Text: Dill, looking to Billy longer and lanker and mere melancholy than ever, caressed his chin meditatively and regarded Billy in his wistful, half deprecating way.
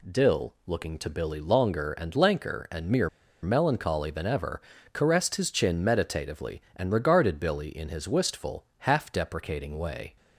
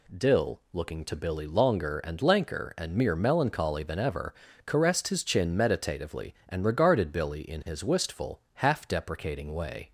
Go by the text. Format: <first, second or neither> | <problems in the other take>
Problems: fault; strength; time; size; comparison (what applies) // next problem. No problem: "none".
second | pauses between "mere" and "melancholy"; slight; at 3.0 s; 0.34 s long